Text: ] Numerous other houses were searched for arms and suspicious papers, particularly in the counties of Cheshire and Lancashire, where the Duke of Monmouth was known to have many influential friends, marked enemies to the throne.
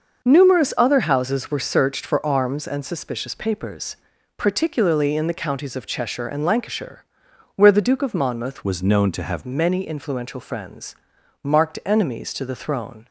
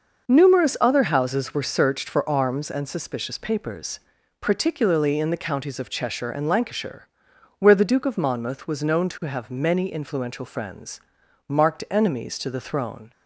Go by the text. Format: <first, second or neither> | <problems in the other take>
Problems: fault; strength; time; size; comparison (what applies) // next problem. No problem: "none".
second | changes voice from "was" to "have"; from 8.6 to 9.4 s; 0.8 s long